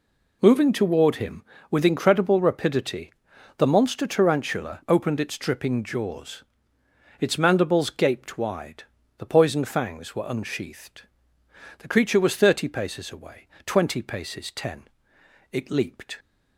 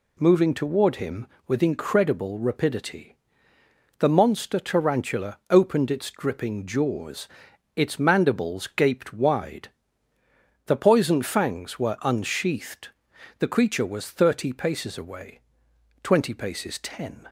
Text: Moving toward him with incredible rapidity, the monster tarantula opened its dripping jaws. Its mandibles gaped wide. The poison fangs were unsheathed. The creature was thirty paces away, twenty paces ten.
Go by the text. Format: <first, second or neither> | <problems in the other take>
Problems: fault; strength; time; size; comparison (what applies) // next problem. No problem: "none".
second | goes on to say "It leaped"; noticeable; from 15.5 s on; 0.68 s long